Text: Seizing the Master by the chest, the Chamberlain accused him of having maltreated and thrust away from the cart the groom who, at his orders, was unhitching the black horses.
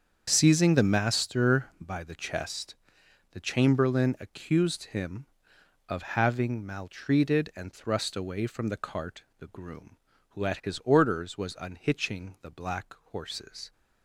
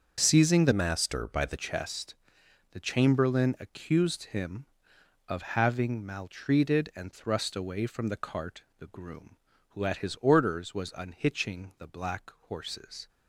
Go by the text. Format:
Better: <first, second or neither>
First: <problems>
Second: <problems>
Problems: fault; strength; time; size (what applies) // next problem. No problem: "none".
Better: first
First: starts louder than the rest; strong; until 1.3 s; 7 dB // pauses between "cart" and "the"; slight; at 9.2 s; 0.16 s long // pauses between "black" and "horses"; slight; at 12.9 s; 0.16 s long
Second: starts louder than the rest; until 1.2 s; 6.5 dB // changes voice from "Master" to "the"; from 0.7 to 1.5 s; 0.8 s long // pauses between "cart" and "the"; slight; at 8.6 s; 0.16 s long // pauses between "black" and "horses"; slight; at 12.3 s; 0.16 s long